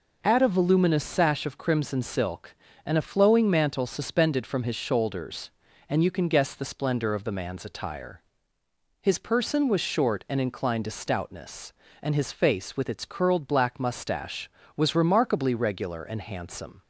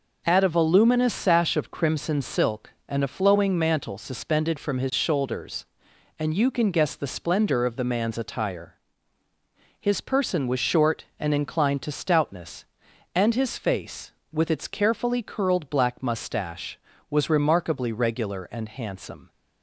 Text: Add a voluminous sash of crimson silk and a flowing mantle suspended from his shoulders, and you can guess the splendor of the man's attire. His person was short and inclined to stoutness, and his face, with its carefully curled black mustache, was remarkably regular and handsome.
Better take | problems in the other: second | skips "carefully"; at 13.0 s

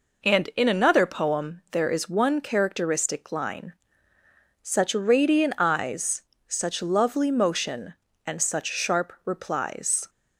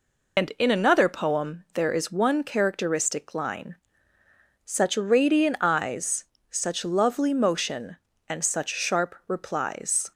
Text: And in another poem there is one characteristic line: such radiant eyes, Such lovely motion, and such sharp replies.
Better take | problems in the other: first | loses the start of "And"; at 0.3 s; 115 ms

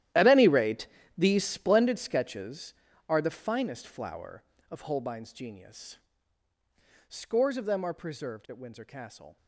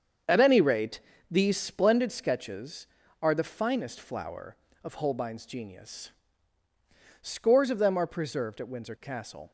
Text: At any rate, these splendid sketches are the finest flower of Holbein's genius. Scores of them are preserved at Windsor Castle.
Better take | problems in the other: second | gets quieter; strong; throughout; 16.5 dB // starts louder than the rest; strong; until 1.4 s; 13 dB; strong in the second

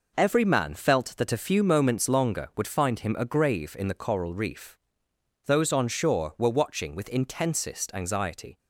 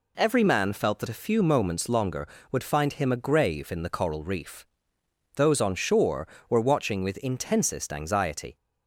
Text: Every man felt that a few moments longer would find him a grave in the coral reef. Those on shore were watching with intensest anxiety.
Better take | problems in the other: second | gets quieter; strong; throughout; 7.5 dB

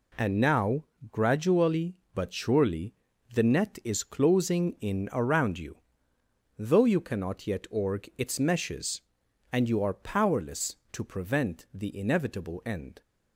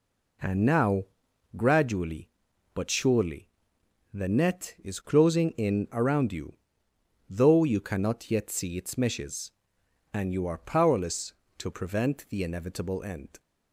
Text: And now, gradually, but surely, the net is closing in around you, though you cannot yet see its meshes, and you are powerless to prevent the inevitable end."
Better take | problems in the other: second | says "org" for "see"; at 7.7 s

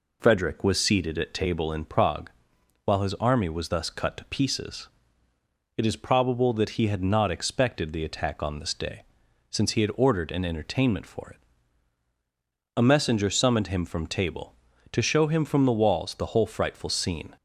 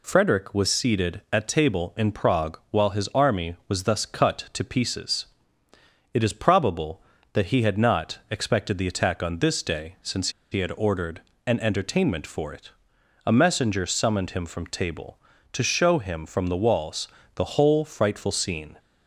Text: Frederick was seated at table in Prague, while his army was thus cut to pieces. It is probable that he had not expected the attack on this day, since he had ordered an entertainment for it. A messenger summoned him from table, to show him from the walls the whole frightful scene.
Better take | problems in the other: first | pauses between "since" and "he"; slight; at 10.2 s; 0.22 s long // pauses between "ordered" and "an"; slight; at 11.2 s; 0.26 s long // pauses between "walls" and "the"; slight; at 17.0 s; 0.28 s long

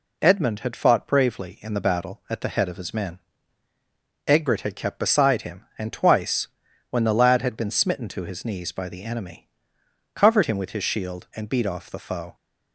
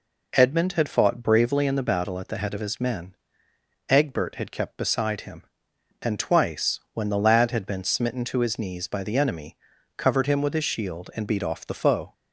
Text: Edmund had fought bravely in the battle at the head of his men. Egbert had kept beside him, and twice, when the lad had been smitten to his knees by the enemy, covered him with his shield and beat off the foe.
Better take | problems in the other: neither | none

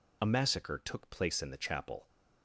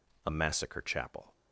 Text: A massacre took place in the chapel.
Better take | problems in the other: first | skips "took place in the"; at 0.8 s

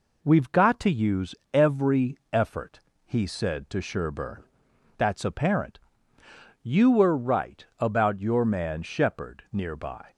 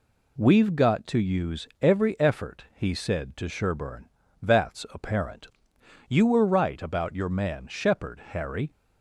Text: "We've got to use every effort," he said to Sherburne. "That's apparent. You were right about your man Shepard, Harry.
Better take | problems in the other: second | pauses between "use" and "every"; slight; at 1.3 s; 0.20 s long // says "Nearby" for "Harry"; at 9.5 s

